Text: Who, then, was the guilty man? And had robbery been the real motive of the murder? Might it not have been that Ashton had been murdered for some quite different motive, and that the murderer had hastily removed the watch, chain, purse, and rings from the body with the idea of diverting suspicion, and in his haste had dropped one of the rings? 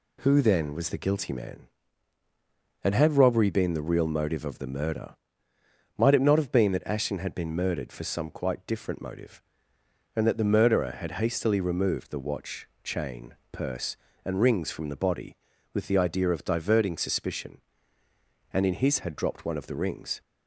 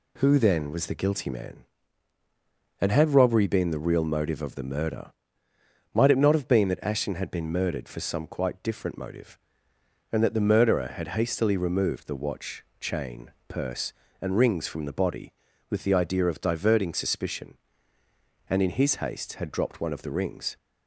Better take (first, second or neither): second